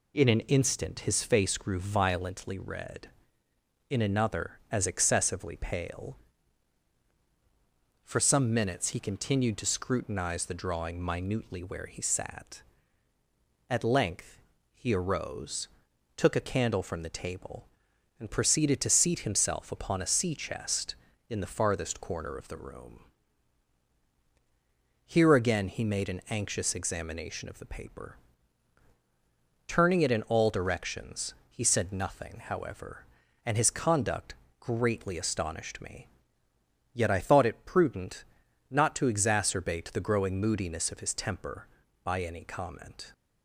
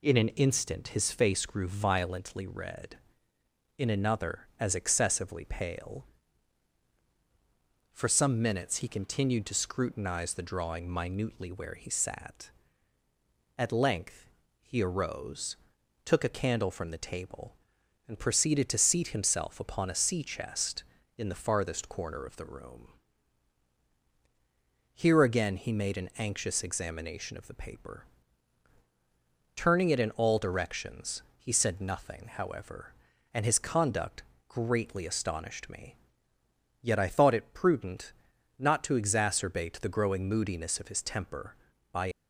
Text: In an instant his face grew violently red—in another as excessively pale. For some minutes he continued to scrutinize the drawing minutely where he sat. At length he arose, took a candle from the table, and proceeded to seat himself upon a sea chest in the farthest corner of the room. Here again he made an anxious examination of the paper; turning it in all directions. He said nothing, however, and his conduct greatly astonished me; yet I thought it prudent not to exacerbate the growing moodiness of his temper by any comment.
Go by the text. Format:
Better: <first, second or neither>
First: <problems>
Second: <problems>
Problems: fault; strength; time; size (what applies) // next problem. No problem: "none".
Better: first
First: pauses between "length" and "he"; slight; at 14.3 s; 0.34 s long // pauses between "conduct" and "greatly"; slight; at 34.3 s; 0.24 s long // pauses between "prudent" and "not"; noticeable; at 38.2 s; 0.48 s long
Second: pauses between "length" and "he"; slight; at 14.2 s; 0.34 s long // pauses between "conduct" and "greatly"; slight; at 34.2 s; 0.24 s long // pauses between "prudent" and "not"; noticeable; at 38.1 s; 0.48 s long // stops before "any comment"; at 42.1 s